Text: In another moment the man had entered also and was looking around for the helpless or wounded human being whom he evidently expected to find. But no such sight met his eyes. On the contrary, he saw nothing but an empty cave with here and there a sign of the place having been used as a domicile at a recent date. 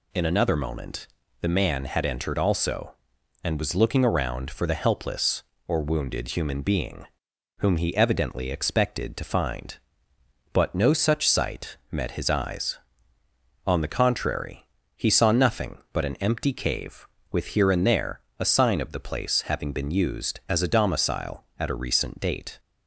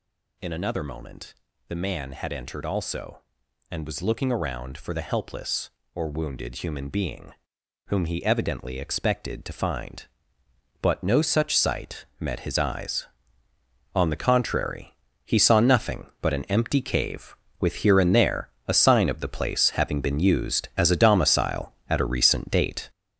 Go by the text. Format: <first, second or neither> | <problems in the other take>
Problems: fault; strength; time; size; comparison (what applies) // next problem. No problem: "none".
first | gets louder; strong; throughout; 7.5 dB // pauses between "moment" and "the"; slight; at 1.3 s; 0.34 s long; slight in the first // pauses between "being" and "whom"; noticeable; at 7.3 s; 0.56 s long; noticeable in the first // pauses between "there" and "a"; slight; at 18.4 s; 0.20 s long; slight in the first